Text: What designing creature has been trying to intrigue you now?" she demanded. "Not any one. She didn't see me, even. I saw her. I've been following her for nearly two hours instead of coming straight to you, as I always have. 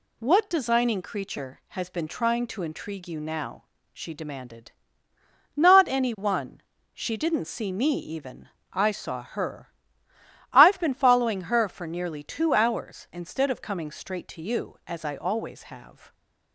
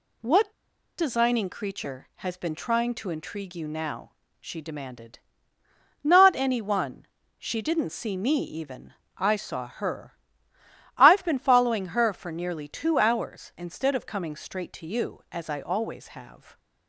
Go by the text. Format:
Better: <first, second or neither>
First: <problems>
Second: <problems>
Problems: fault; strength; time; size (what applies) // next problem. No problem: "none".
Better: first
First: none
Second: pauses between "What" and "designing"; at 0.5 s; 0.45 s long